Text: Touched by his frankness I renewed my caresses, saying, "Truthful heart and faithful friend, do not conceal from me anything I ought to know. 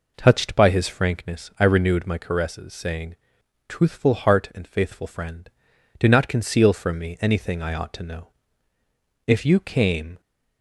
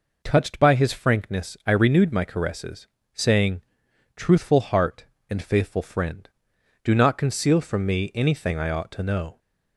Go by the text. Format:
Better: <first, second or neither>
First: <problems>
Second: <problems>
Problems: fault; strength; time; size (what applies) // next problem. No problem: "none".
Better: second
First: goes on to say "If you came"; noticeable; from 9.2 s on; 0.94 s long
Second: none